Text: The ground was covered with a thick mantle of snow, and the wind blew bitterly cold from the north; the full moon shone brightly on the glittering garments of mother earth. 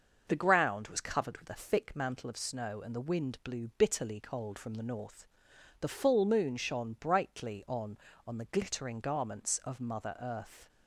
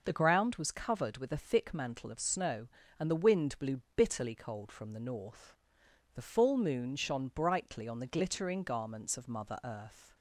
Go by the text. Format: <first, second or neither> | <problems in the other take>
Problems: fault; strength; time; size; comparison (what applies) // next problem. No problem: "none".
second | starts louder than the rest; noticeable; until 1.2 s; 6 dB // says "on" twice; at 8.2 s